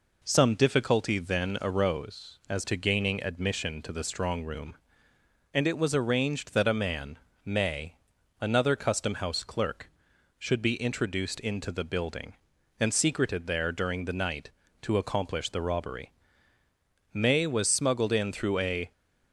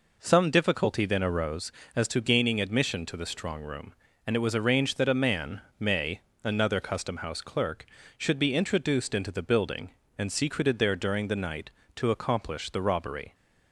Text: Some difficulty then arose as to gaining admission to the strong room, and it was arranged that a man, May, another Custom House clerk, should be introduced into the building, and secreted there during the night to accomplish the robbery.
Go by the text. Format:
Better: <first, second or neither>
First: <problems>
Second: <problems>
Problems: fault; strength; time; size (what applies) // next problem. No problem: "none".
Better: second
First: goes on to say "May was smuggled in through a"; strong; from 17.1 s on; 1.8 s long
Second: none